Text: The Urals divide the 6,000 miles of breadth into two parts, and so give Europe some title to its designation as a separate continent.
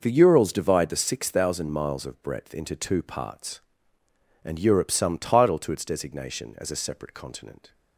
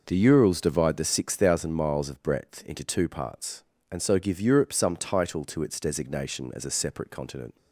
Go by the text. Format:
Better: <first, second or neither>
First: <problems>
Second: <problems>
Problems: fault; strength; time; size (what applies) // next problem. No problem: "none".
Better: second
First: skips "so give"; at 4.5 s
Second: none